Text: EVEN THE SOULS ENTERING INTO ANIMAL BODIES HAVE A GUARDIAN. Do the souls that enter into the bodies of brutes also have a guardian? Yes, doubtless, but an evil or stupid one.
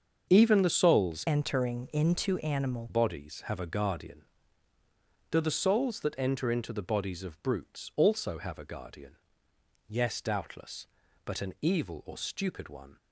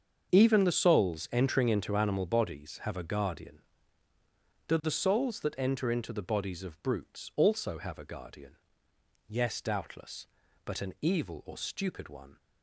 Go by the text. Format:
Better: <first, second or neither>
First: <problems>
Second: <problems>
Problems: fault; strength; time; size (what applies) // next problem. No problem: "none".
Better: second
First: starts louder than the rest; until 1.3 s; 7 dB // changes voice from "ENTERING" to "ANIMAL"; from 1.2 to 2.8 s; 1.6 s long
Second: starts louder than the rest; until 1.3 s; 7 dB